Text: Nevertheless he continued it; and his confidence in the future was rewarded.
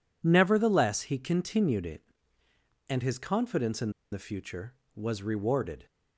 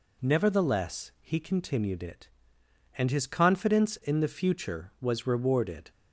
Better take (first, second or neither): second